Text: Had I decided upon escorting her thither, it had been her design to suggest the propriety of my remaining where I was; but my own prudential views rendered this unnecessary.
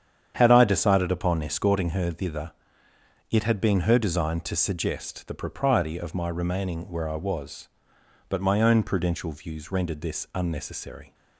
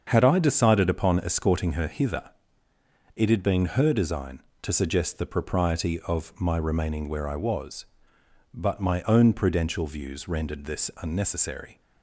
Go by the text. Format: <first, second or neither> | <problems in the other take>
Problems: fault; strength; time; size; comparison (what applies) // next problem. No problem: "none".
first | starts louder than the rest; until 1.0 s; 7 dB; strong in the first // says "hither" for "thither"; at 1.8 s